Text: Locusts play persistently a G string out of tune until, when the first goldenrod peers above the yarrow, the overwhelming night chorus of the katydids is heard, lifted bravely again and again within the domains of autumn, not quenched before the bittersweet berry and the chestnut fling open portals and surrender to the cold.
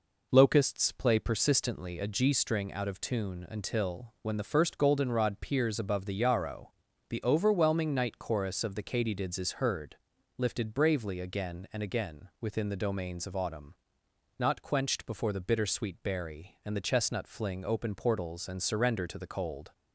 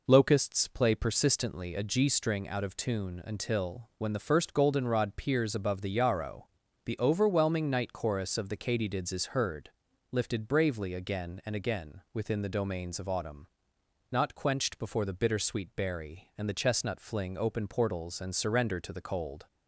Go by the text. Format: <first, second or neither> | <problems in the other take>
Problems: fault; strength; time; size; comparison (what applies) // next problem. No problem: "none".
neither | none